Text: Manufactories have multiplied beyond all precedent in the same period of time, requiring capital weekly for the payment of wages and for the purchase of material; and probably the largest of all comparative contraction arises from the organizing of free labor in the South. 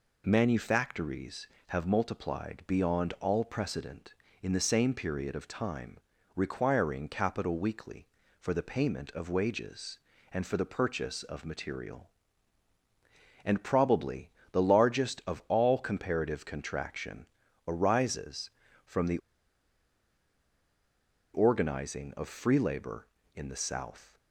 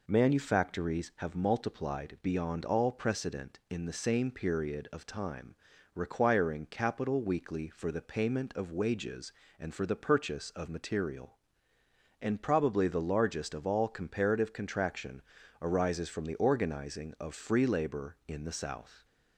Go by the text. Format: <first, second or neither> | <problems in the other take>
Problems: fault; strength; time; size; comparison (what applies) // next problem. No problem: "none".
second | pauses between "probably" and "the"; slight; at 14.3 s; 0.20 s long // pauses between "contraction" and "arises"; at 17.2 s; 0.40 s long; also in the second // pauses between "the" and "organizing"; strong; at 19.1 s; 2.1 s long